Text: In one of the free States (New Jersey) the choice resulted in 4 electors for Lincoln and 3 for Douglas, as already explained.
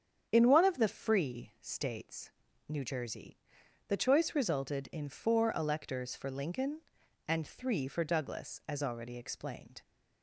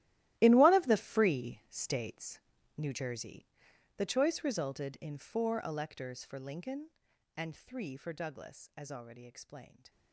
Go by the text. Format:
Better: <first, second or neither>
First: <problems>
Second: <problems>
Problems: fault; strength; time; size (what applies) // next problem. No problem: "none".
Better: first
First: starts louder than the rest; strong; until 1.3 s; 8 dB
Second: gets quieter; strong; throughout; 16.5 dB // starts louder than the rest; strong; until 1.3 s; 15 dB